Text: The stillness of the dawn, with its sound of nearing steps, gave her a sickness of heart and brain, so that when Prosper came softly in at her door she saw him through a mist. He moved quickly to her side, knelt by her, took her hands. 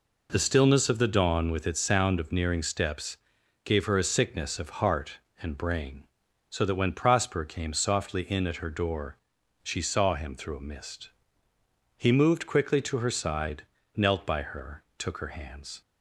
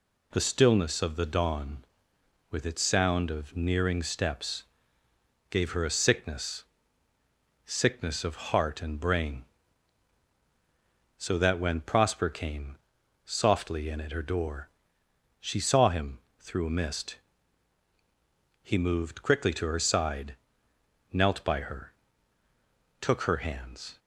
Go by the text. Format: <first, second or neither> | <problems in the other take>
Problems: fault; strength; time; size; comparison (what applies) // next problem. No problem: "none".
first | says "sickness" twice; at 7.6 s // pauses between "came" and "softly"; noticeable; at 12.7 s; 0.48 s long // pauses between "door" and "she"; noticeable; at 14.6 s; 0.72 s long; also in the first // pauses between "him" and "through"; slight; at 16.1 s; 0.20 s long